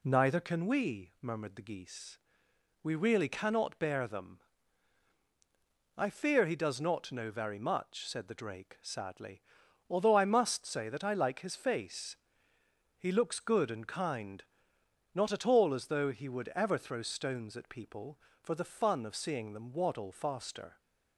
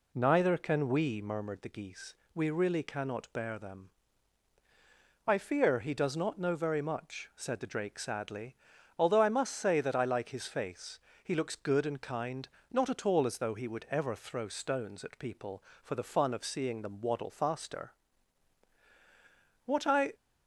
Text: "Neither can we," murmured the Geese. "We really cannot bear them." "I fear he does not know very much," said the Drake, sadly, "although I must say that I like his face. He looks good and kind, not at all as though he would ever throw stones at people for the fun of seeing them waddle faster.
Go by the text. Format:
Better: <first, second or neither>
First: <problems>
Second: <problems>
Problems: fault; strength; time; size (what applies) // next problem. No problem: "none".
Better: first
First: none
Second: goes on to say "What I"; from 19.6 s on; 0.50 s long